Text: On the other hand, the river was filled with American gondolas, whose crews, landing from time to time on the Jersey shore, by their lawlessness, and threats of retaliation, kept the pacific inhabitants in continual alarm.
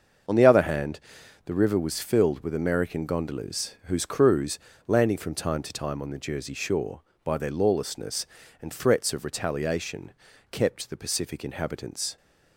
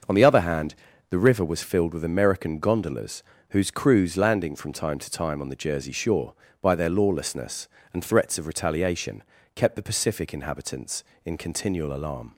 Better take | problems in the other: second | starts louder than the rest; until 1.7 s; 6.5 dB; noticeable in the second // stops before "in continual alarm"; at 12.1 s

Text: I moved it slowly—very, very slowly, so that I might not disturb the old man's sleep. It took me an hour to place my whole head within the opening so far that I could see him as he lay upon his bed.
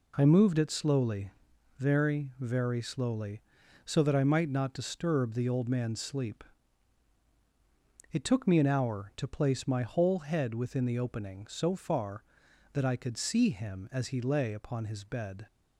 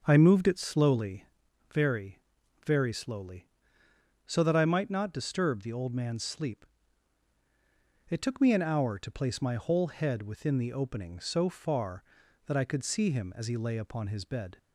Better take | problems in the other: first | starts louder than the rest; until 1.4 s; 7 dB

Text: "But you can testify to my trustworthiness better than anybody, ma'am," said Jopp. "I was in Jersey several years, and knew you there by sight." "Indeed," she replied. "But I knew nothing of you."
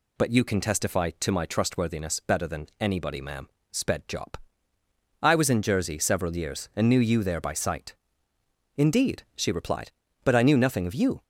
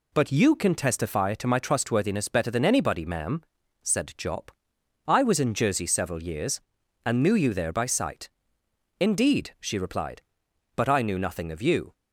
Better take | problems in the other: second | says "sped" for "said"; at 3.7 s

